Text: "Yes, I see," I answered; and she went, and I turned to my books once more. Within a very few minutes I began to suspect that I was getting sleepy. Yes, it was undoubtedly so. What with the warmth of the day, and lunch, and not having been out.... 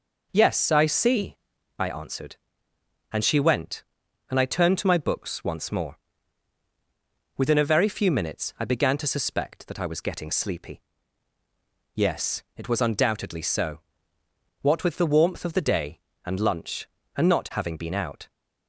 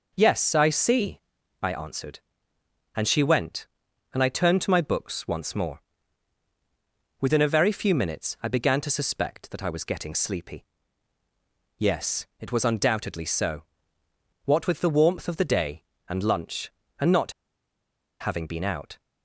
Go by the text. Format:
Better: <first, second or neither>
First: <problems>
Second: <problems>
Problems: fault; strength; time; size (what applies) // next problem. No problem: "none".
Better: first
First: none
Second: pauses between "not" and "having"; noticeable; at 17.3 s; 0.88 s long